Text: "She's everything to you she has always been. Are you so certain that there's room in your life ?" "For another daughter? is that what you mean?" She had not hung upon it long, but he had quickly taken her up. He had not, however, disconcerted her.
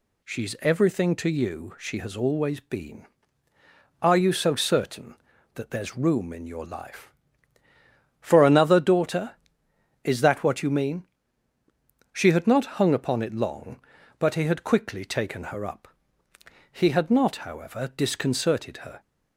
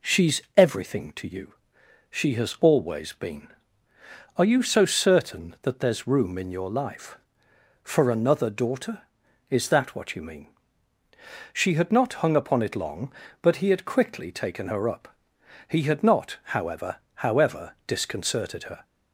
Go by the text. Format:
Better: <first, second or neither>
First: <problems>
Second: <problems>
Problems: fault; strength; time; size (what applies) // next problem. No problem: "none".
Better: first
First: none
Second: pauses between "She's" and "everything"; slight; at 0.4 s; 0.16 s long // pauses between "you" and "she"; noticeable; at 1.5 s; 0.56 s long // says "however" twice; at 17.1 s